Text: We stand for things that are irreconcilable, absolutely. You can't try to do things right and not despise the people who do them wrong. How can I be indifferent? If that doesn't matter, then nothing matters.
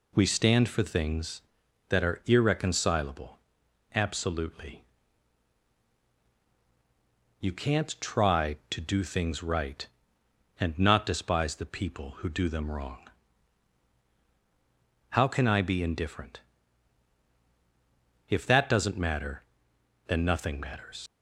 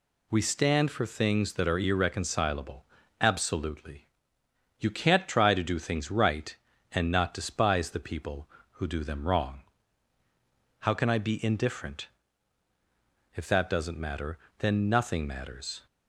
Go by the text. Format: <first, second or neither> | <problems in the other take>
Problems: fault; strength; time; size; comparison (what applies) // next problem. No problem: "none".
second | leaves "matters" unfinished; at 21.0 s; 80 ms